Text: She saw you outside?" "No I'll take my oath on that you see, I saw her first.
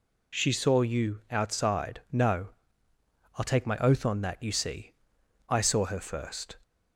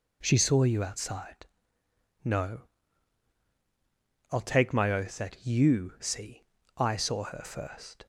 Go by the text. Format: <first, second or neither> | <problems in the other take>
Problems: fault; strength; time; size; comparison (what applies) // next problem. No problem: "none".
first | pauses between "No" and "I'll"; strong; at 2.6 s; 1.6 s long; noticeable in the first // skips "on"; at 5.1 s